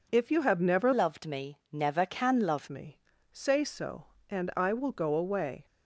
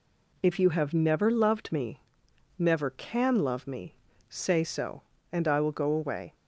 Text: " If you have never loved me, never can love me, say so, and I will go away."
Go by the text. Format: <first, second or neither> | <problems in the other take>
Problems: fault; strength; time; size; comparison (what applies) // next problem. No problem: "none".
second | changes voice from "loved" to "love"; from 0.9 to 2.6 s; 1.7 s long